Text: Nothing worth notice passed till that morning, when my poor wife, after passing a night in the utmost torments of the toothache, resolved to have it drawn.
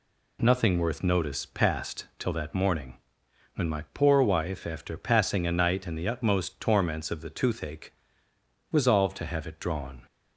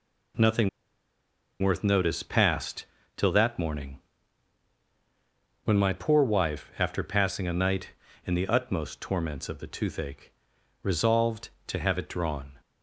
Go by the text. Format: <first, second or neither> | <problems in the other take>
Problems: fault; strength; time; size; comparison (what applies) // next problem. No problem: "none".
first | pauses between "Nothing" and "worth"; noticeable; at 0.6 s; 0.92 s long // pauses between "passed" and "till"; slight; at 2.8 s; 0.32 s long